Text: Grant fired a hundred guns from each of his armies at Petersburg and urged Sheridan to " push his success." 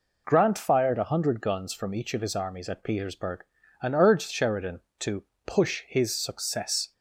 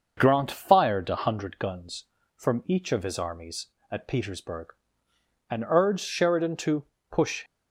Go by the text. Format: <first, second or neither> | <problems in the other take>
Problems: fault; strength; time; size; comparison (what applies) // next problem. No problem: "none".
first | starts louder than the rest; until 1.1 s; 6.5 dB // stops before "his success"; at 7.4 s